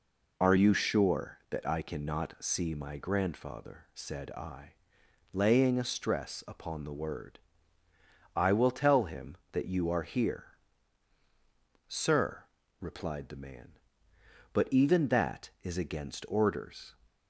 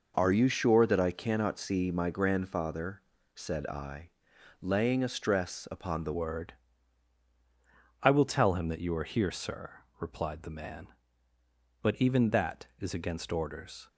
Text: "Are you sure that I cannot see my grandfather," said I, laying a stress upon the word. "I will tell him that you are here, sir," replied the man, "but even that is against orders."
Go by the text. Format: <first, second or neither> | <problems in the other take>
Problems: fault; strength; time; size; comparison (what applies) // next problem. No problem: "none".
first | changes voice at "word"; from 6.1 s on; 7.7 s long